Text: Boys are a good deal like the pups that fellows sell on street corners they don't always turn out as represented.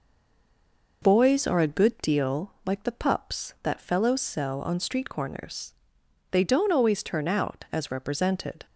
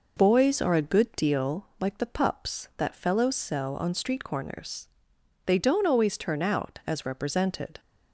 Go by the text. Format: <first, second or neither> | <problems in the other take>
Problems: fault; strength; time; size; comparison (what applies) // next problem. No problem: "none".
second | stays silent before the first word; until 1.0 s; 1.0 s long // pauses between "corners" and "they"; noticeable; at 5.7 s; 0.58 s long; noticeable in the second